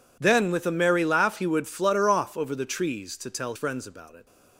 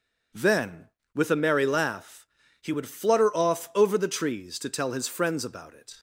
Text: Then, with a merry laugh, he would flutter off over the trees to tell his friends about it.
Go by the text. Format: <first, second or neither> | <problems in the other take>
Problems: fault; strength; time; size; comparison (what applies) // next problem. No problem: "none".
second | skips "his"; at 3.5 s